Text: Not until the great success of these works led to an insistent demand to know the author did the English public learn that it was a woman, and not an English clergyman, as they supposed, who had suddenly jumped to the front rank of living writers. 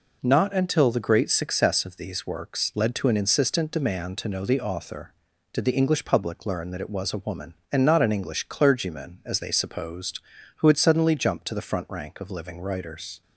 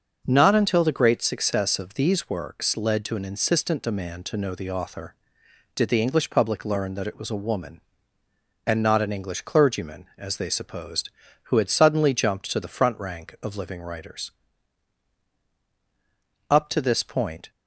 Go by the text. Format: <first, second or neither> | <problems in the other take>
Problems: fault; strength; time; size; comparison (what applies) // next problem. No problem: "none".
first | starts louder than the rest; noticeable; until 1.2 s; 6 dB // goes on to say "Up to this point"; noticeable; from 16.5 s on; 1.0 s long